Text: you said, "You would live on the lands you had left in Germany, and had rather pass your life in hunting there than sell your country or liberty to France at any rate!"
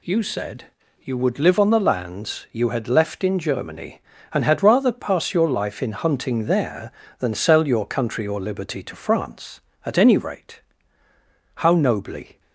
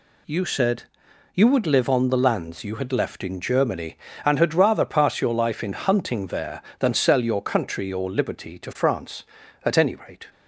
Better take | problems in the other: second | goes on to say "How nobly"; noticeable; from 11.5 s on; 0.86 s long

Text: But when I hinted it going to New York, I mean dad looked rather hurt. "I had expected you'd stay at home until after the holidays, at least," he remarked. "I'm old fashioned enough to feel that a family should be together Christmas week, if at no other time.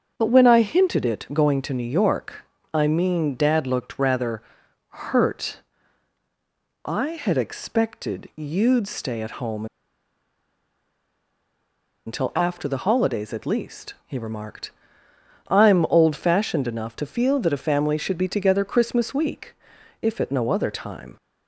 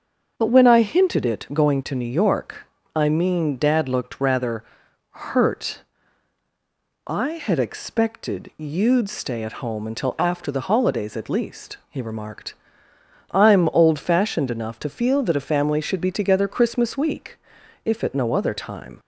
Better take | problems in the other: second | starts louder than the rest; until 1.1 s; 7 dB; also in the second // pauses between "rather" and "hurt"; noticeable; at 4.4 s; 0.46 s long; noticeable in the second // pauses between "home" and "until"; strong; at 9.6 s; 2.4 s long

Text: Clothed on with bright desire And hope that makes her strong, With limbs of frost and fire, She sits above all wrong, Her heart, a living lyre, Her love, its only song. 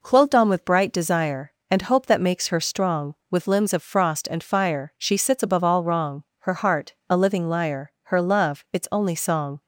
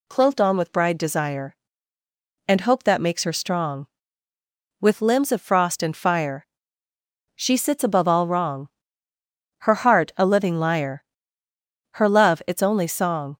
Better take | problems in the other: first | says "bride" for "bright"; at 0.7 s

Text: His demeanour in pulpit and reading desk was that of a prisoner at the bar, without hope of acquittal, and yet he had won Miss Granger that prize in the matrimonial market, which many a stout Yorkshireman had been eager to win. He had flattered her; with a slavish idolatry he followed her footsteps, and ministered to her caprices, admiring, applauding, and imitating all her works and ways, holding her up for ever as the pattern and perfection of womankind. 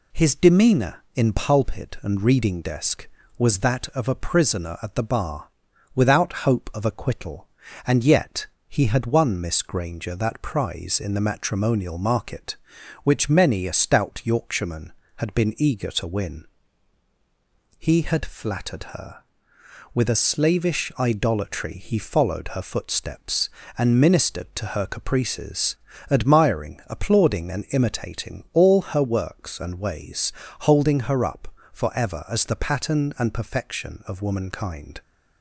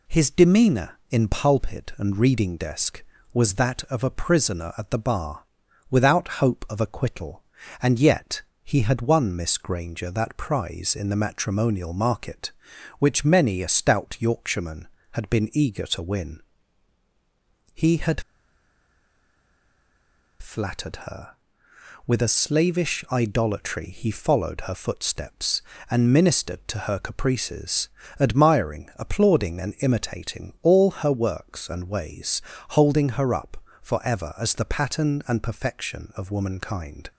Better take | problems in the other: first | pauses between "yet" and "he"; slight; at 8.4 s; 0.22 s long; slight in the first // pauses between "had" and "flattered"; strong; at 18.2 s; 2.1 s long

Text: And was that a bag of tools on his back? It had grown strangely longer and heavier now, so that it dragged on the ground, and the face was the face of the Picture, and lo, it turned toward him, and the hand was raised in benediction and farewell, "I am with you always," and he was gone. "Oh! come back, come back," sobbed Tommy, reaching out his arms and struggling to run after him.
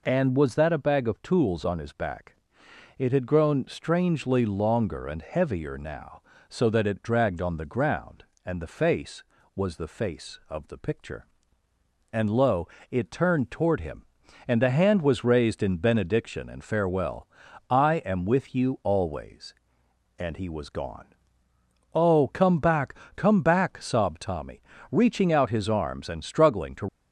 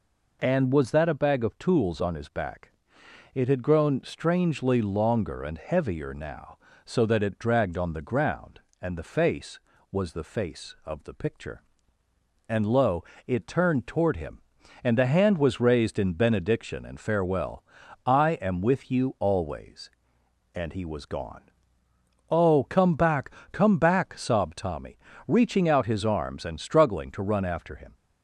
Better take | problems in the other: second | stops before "run after him"; at 26.8 s

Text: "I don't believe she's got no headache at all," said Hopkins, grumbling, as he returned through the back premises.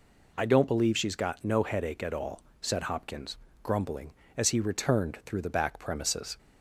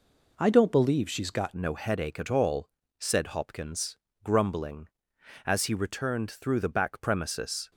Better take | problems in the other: first | changes voice at "no"; from 1.5 s on; 6.2 s long

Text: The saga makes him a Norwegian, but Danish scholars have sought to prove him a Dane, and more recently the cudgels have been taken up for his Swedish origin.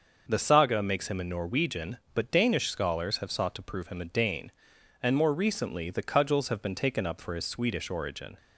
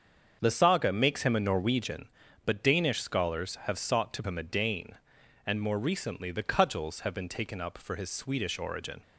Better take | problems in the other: first | starts louder than the rest; until 1.4 s; 7 dB; also in the first // skips "prove"; at 4.2 s

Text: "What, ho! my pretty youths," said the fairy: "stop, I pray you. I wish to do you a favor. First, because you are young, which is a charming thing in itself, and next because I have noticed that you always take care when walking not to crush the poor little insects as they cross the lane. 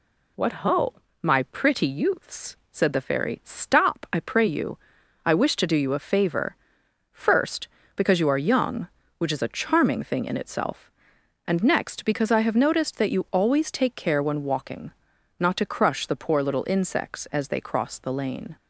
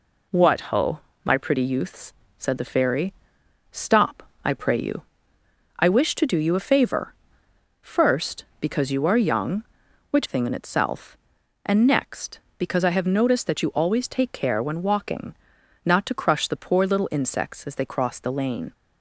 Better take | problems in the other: first | skips "is a charming"; at 10.2 s // pauses between "walking" and "not"; noticeable; at 15.3 s; 0.50 s long; noticeable in the first

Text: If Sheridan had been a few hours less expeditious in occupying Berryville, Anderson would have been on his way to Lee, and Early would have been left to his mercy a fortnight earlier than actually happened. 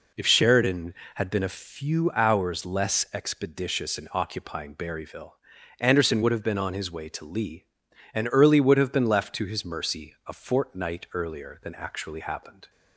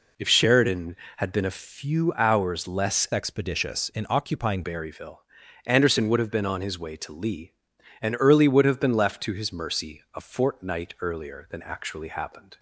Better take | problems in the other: first | changes voice from "expeditious" to "occupying"; from 3.1 to 4.6 s; 1.5 s long

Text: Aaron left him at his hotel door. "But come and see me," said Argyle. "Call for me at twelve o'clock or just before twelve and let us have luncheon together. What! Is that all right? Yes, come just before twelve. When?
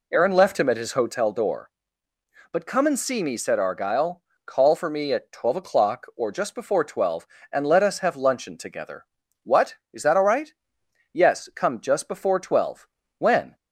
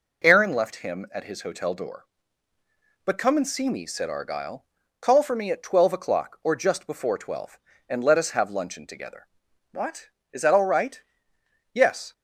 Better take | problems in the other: first | stops before "come just before twelve When"; at 12.1 s

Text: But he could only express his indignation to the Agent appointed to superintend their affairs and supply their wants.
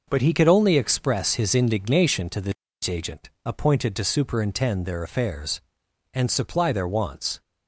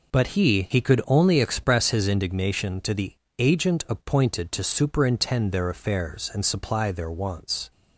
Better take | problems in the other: first | says "he" twice; at 0.6 s // pauses between "the" and "Agent"; slight; at 3.1 s; 0.26 s long; slight in the first

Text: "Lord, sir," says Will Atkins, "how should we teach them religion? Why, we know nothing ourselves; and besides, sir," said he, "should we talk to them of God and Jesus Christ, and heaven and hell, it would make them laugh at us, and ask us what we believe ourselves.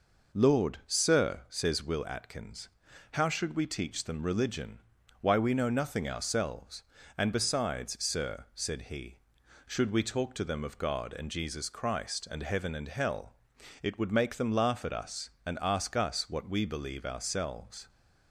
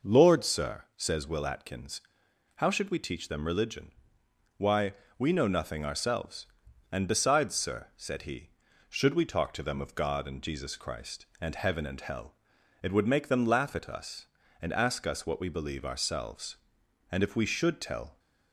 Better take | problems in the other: first | goes on to say "And if we should tell"; noticeable; from 17.1 s on; 1.0 s long

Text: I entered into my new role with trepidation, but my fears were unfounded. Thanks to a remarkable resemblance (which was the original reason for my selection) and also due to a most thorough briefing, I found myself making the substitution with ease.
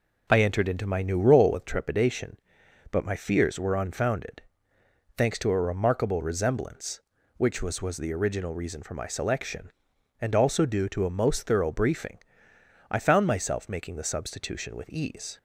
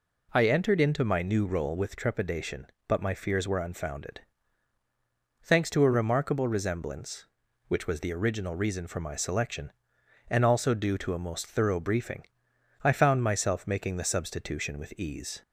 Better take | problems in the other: second | says "was" twice; at 7.7 s

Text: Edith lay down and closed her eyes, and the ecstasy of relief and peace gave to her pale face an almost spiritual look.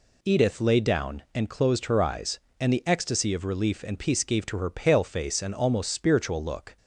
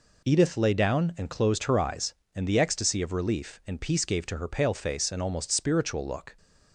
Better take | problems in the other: neither | none

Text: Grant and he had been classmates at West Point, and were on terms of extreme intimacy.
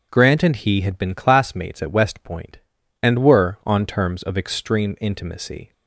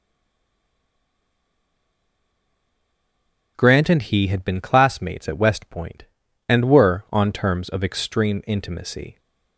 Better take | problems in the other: first | stays silent before the first word; strong; until 3.5 s; 3.5 s long // starts louder than the rest; until 4.5 s; 6.5 dB; also in the first

